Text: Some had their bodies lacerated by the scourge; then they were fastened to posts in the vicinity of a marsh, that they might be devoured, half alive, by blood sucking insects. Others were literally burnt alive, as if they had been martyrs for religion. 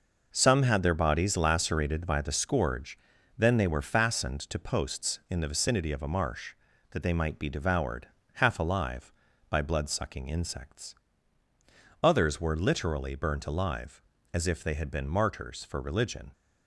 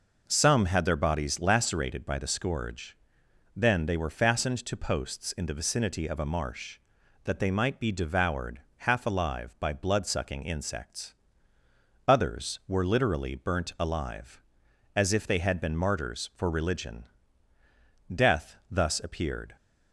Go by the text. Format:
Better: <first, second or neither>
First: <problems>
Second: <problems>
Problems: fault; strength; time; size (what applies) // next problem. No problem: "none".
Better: first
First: none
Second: goes on to say "Death thus appeared"; from 18.1 s on; 1.4 s long